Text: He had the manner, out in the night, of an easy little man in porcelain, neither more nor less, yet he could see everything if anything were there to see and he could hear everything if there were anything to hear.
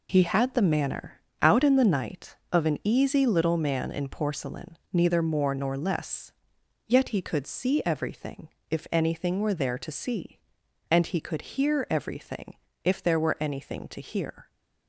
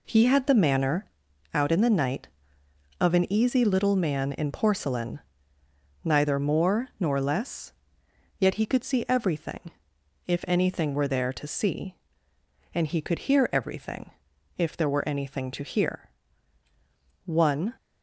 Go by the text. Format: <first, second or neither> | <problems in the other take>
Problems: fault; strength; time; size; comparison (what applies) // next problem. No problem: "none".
first | pauses between "everything" and "if"; noticeable; at 9.7 s; 0.56 s long; slight in the first // pauses between "everything" and "if"; noticeable; at 14.0 s; 0.48 s long; slight in the first // goes on to say "One"; slight; from 17.2 s on; 0.48 s long